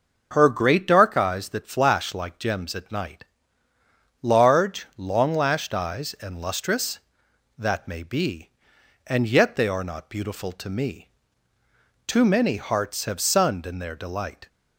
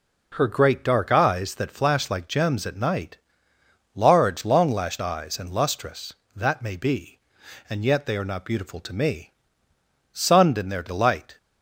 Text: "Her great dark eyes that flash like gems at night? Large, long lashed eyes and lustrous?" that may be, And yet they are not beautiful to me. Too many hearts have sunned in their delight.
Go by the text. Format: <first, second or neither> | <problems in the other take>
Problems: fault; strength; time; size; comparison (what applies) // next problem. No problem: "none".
first | skips "Too many hearts have"; at 9.7 s